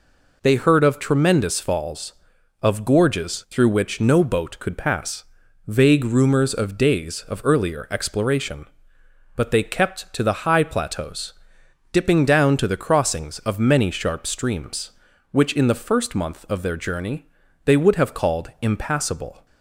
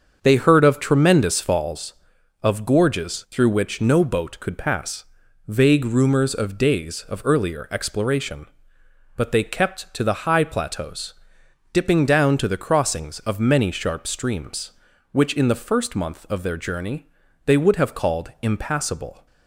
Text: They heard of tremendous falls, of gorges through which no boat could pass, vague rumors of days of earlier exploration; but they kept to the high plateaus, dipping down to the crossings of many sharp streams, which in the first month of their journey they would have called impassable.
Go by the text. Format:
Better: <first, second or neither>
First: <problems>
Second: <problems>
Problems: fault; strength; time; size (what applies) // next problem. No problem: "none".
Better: first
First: pauses between "journey" and "they"; at 17.2 s; 0.40 s long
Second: starts louder than the rest; until 1.9 s; 7 dB // pauses between "journey" and "they"; at 17.0 s; 0.40 s long